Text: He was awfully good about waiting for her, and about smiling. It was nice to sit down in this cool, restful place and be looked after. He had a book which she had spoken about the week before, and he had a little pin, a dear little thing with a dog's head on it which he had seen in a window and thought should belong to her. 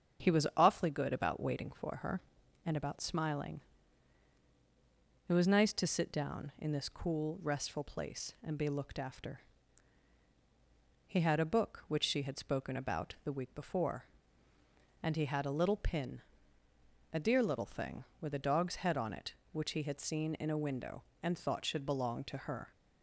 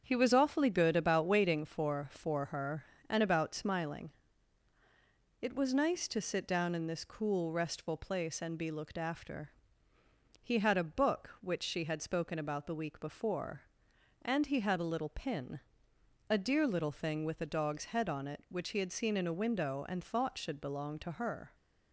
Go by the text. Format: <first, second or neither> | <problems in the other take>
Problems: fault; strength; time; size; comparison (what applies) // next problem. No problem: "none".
first | starts louder than the rest; strong; until 1.0 s; 7 dB; strong in the first // says "for" twice; at 2.1 s